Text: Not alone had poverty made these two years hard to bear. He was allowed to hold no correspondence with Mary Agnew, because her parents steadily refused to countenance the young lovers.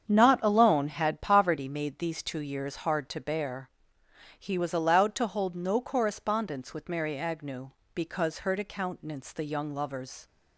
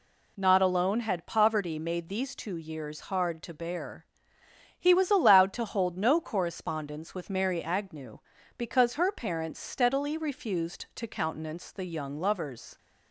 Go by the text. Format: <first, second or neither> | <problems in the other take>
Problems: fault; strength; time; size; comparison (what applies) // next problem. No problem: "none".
second | starts louder than the rest; strong; until 1.1 s; 7.5 dB // skips "parents steadily refused"; at 8.5 s